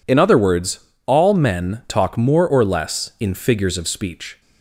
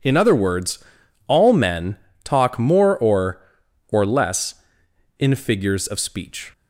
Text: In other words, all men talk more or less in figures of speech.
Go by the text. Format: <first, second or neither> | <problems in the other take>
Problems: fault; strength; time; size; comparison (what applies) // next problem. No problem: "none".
first | pauses between "men" and "talk"; slight; at 1.9 s; 0.26 s long // says "or" twice; at 3.8 s